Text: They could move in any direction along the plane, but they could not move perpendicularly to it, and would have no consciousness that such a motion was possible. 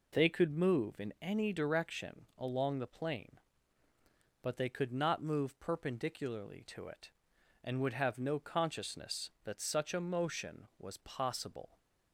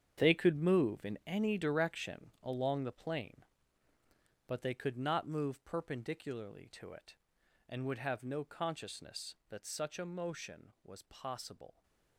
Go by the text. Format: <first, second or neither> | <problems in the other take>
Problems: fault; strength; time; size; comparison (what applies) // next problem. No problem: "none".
first | gets quieter; strong; throughout; 12.5 dB